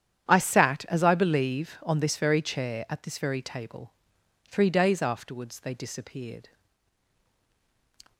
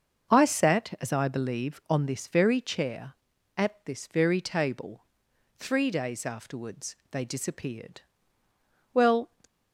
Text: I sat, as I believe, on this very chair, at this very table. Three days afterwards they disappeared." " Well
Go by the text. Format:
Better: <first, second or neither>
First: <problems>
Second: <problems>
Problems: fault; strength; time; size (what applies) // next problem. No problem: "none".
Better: second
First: starts louder than the rest; strong; until 1.3 s; 10.5 dB // stops before "Well"; at 8.1 s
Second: starts louder than the rest; until 1.4 s; 7 dB